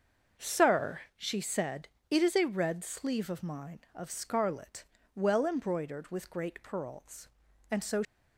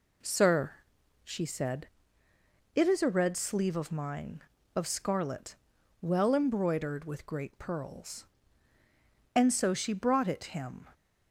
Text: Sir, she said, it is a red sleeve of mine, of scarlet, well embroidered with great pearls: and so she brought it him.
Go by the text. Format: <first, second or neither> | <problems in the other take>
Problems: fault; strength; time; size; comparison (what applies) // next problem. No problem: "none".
second | starts louder than the rest; noticeable; until 1.5 s; 6 dB // stops before "she brought it him"; at 8.0 s